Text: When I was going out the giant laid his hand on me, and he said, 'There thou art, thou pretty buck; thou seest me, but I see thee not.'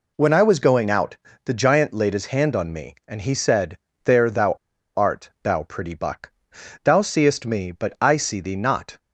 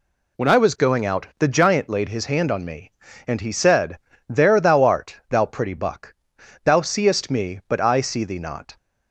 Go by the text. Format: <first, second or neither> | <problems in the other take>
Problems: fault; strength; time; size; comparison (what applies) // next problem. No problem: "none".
second | pauses between "out" and "the"; slight; at 1.1 s; 0.28 s long // pauses between "thou" and "art"; at 4.5 s; 0.43 s long